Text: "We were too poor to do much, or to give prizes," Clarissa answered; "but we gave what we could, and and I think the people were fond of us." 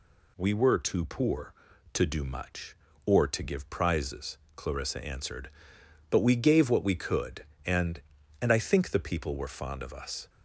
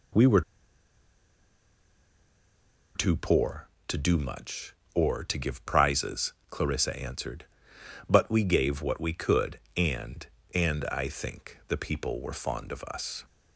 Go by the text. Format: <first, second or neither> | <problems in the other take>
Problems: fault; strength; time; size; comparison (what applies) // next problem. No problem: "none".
first | pauses between "were" and "too"; strong; at 0.4 s; 2.5 s long